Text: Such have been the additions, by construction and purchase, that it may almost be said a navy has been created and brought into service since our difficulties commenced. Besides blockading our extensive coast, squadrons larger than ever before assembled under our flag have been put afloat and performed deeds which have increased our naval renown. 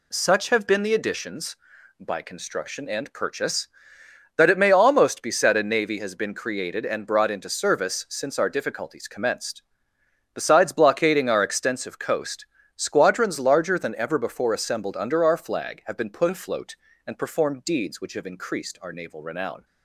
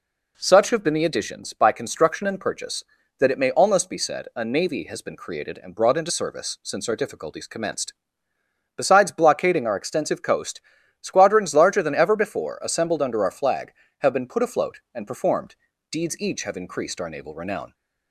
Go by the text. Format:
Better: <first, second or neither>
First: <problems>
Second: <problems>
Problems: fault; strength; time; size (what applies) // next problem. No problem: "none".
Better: first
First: none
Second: pauses between "performed" and "deeds"; slight; at 15.5 s; 0.34 s long // says "each" for "which"; at 16.1 s